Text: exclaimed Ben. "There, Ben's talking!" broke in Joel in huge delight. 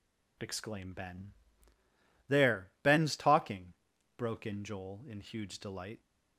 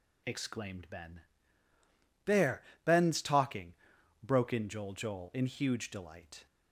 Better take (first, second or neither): first